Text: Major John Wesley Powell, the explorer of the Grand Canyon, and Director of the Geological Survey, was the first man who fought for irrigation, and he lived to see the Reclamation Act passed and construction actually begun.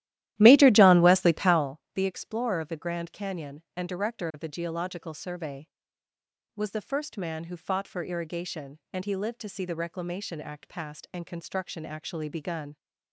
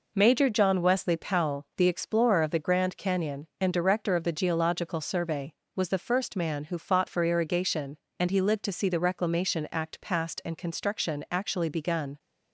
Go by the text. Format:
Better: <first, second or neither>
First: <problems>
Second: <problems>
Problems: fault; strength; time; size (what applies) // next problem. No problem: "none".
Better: second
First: starts louder than the rest; strong; until 1.8 s; 14 dB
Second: none